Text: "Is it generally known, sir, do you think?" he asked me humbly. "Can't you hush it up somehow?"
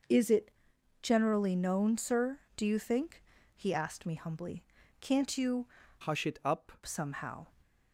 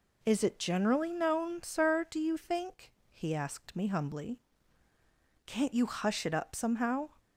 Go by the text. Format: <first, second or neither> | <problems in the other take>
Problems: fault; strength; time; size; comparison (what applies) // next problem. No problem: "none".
second | pauses between "it" and "generally"; noticeable; at 0.4 s; 0.52 s long // changes voice from "hush" to "up"; from 6.0 to 6.7 s; 0.7 s long